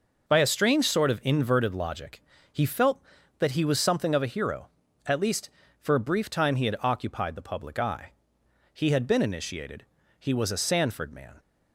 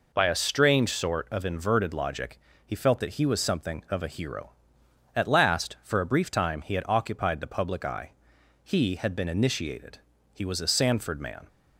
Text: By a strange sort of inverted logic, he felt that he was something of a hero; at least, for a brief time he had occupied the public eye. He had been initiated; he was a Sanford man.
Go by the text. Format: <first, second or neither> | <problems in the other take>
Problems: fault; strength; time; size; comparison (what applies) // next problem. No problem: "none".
first | says "last" for "least"; at 5.2 s